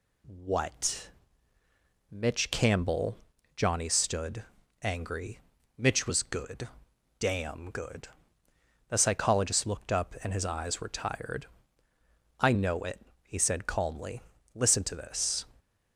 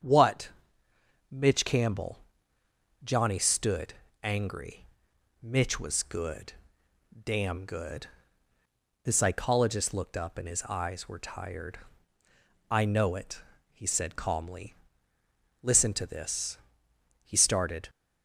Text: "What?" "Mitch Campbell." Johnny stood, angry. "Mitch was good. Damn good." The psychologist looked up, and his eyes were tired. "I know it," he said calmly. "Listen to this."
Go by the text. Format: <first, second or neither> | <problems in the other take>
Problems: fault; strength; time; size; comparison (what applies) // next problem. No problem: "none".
first | starts louder than the rest; strong; until 1.8 s; 7.5 dB // goes on to say "He started"; noticeable; from 17.2 s on; 0.66 s long